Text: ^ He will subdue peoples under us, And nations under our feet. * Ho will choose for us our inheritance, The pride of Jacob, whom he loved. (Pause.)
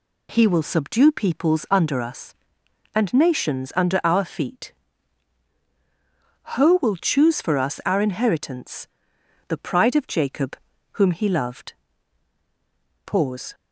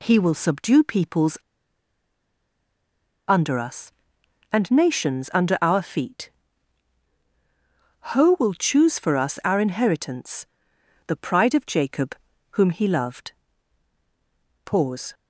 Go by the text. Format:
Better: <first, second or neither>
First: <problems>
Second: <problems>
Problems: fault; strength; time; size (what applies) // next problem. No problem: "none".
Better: first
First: none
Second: pauses between "peoples" and "under"; strong; at 1.3 s; 1.9 s long